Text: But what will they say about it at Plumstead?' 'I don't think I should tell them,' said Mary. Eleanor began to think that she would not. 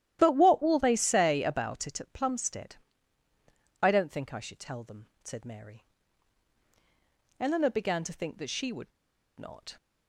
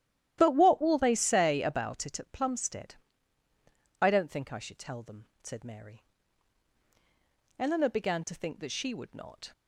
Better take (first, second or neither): second